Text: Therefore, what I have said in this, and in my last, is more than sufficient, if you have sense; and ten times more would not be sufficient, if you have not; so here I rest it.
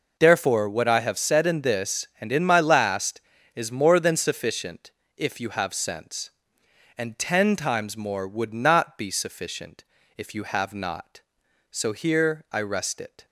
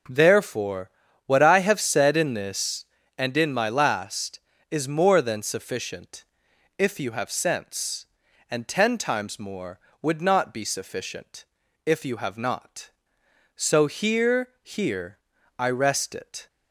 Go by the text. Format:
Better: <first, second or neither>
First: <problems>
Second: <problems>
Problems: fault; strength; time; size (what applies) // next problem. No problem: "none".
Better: first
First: none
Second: starts louder than the rest; until 1.4 s; 6 dB // says "here" twice; at 14.6 s